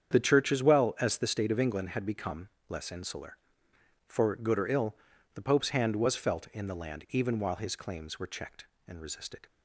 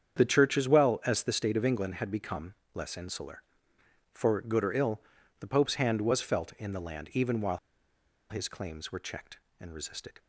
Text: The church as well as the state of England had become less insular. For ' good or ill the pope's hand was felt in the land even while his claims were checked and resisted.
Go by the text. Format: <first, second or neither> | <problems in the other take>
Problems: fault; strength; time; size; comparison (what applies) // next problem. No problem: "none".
first | starts louder than the rest; strong; until 1.2 s; 8 dB; strong in the first // pauses between "become" and "less"; slight; at 2.5 s; 0.18 s long; slight in the first // pauses between "ill" and "the"; at 4.9 s; 0.42 s long; also in the first // pauses between "while" and "his"; noticeable; at 7.5 s; 0.72 s long